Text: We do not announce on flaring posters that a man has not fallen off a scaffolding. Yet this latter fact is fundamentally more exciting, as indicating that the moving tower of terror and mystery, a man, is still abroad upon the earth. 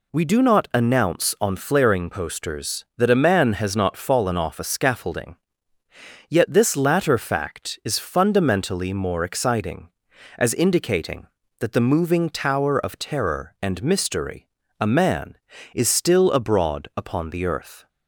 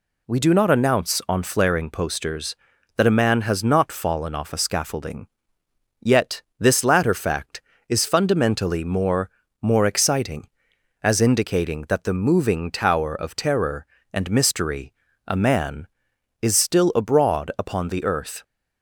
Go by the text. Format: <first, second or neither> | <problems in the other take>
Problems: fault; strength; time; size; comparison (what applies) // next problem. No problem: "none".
first | pauses between "Yet" and "this"; slight; at 6.4 s; 0.16 s long // says "more" twice; at 9.6 s